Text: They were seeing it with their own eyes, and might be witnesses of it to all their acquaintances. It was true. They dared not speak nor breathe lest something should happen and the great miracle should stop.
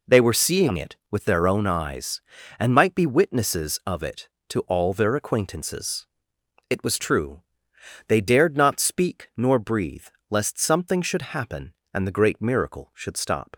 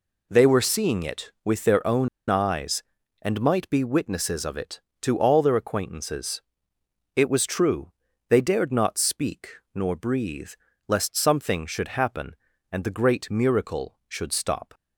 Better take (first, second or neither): first